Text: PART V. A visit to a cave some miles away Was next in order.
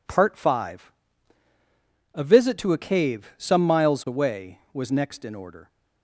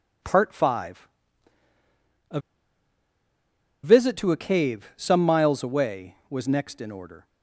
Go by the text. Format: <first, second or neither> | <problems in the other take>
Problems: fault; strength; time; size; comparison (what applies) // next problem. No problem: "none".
first | pauses between "A" and "visit"; strong; at 2.3 s; 1.4 s long